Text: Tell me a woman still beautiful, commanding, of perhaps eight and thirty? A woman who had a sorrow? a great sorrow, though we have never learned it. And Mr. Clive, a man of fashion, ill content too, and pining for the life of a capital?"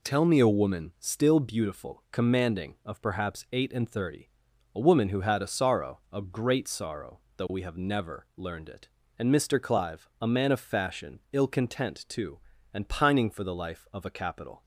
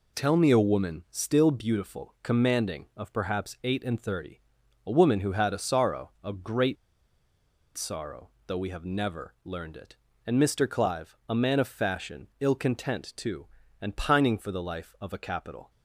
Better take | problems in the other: first | pauses between "great" and "sorrow"; at 6.7 s; 1.0 s long

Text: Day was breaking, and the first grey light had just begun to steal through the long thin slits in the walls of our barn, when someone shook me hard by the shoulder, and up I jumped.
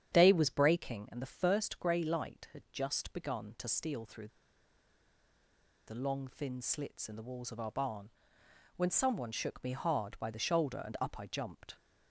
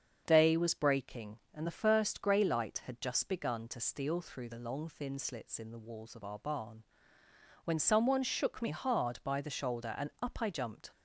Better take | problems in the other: second | starts louder than the rest; strong; until 1.1 s; 9 dB; strong in the second // pauses between "through" and "the"; strong; at 4.2 s; 1.5 s long

